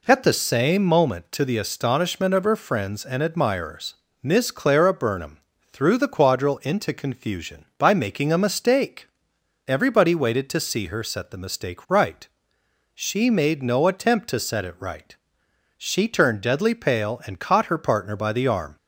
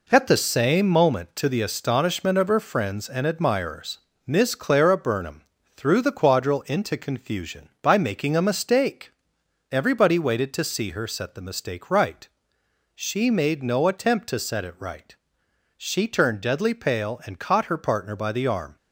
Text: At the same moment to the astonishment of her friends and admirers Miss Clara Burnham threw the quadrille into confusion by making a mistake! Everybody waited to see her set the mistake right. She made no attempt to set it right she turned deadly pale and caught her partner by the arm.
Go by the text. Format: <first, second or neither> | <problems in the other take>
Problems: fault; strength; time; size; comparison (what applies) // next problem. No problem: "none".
first | gets quieter; noticeable; throughout; 5.5 dB // pauses between "admirers" and "Miss"; slight; at 3.9 s; 0.26 s long; slight in the first // pauses between "Burnham" and "threw"; slight; at 5.4 s; 0.32 s long; slight in the first // pauses between "right" and "she"; noticeable; at 15.1 s; 0.64 s long; noticeable in the first